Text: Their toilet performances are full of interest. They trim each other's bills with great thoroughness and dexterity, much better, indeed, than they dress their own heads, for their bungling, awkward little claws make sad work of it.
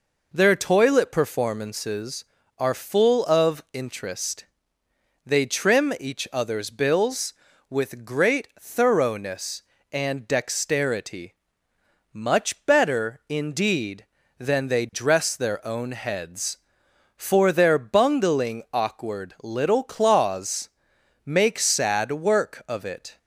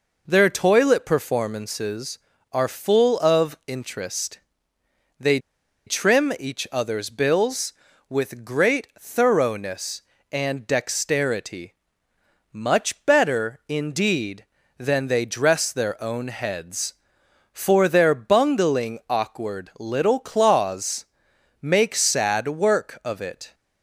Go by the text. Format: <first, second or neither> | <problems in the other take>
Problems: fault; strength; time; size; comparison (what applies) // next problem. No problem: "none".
first | pauses between "They" and "trim"; noticeable; at 5.3 s; 0.48 s long // pauses between "claws" and "make"; noticeable; at 21.0 s; 0.56 s long; noticeable in the first